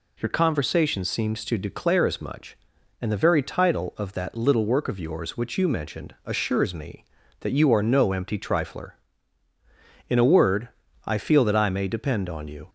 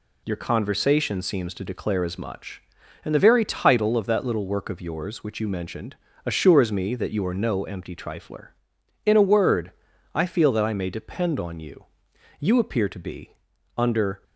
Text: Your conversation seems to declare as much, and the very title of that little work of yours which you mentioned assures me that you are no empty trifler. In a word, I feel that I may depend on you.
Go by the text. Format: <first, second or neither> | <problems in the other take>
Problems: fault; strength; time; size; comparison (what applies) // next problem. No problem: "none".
first | pauses between "mentioned" and "assures"; slight; at 5.9 s; 0.30 s long // goes on to say "You appear to be under"; strong; from 12.3 s on; 1.8 s long